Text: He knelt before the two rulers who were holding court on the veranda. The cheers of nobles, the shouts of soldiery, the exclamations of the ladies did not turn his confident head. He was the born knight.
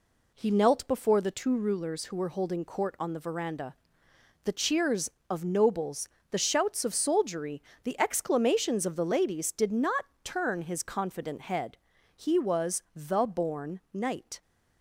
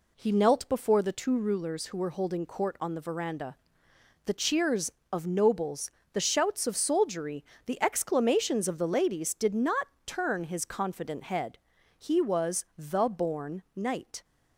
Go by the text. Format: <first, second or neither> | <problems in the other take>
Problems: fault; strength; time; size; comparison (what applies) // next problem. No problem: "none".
neither | pauses between "not" and "turn"; slight; the same in both